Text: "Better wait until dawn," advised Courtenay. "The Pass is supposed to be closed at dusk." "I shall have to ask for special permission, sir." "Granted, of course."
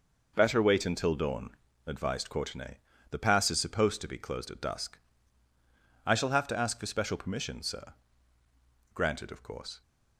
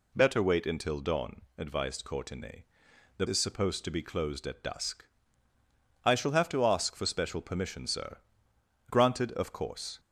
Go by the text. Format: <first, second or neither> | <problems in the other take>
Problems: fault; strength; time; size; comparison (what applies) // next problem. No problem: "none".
first | skips "Pass"; at 3.2 s